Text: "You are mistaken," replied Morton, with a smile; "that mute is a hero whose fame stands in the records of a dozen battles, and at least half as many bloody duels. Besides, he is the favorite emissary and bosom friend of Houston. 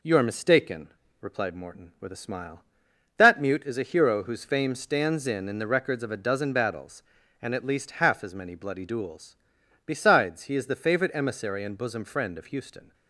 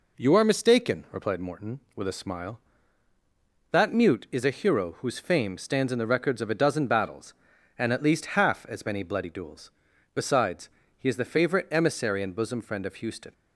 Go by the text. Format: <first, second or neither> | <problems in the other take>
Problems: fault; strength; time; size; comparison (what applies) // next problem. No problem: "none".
second | says "in" twice; at 5.4 s